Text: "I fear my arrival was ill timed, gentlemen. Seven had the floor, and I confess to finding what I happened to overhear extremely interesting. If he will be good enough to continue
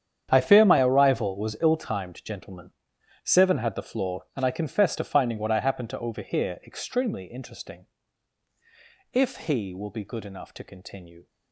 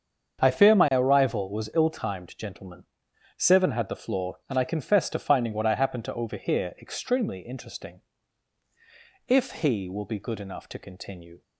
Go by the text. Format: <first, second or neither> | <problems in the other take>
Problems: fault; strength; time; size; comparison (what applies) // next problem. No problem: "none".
second | gets quieter; strong; throughout; 15.5 dB // starts louder than the rest; strong; until 1.3 s; 8.5 dB; strong in the second